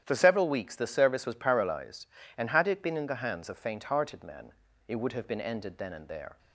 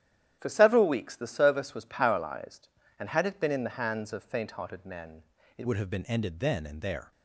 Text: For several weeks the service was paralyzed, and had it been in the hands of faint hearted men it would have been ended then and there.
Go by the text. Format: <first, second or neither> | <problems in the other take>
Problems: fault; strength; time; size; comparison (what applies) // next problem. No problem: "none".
first | starts louder than the rest; strong; until 1.4 s; 11 dB; strong in the first // pauses between "men" and "it"; slight; at 5.2 s; 0.34 s long; also in the first // changes voice at "would"; from 5.6 s on; 1.5 s long